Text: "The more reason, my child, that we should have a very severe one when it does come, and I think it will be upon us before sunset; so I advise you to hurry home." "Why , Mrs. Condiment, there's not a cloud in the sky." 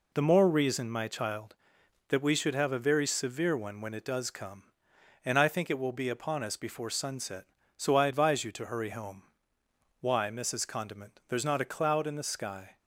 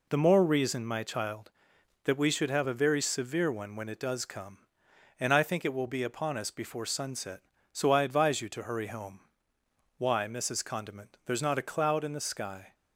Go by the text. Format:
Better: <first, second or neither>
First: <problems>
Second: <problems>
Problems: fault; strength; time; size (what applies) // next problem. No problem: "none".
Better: neither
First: none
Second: none